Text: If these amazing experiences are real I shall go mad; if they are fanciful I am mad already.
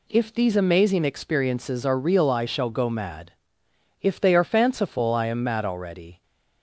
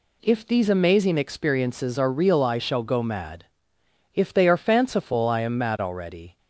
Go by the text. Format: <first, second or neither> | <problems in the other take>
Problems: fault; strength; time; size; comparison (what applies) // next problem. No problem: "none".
neither | none